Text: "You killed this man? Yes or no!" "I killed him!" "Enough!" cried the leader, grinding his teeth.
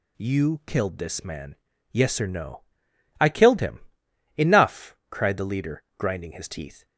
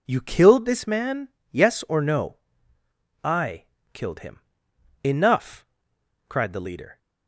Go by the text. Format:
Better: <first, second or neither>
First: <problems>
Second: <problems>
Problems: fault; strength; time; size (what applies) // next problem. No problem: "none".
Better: first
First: none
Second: pauses between "I" and "killed"; slight; at 3.6 s; 0.26 s long // stops before "grinding his teeth"; at 6.9 s